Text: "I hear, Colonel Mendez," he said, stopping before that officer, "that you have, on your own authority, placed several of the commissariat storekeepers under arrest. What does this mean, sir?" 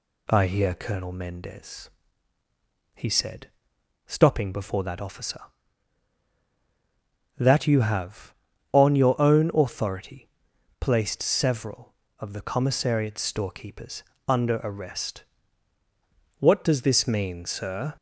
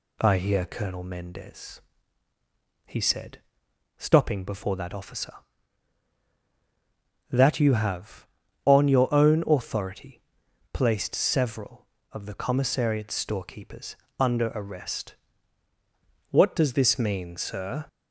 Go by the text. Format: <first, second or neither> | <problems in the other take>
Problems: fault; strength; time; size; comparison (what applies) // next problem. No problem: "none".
neither | pauses between "storekeepers" and "under"; slight; the same in both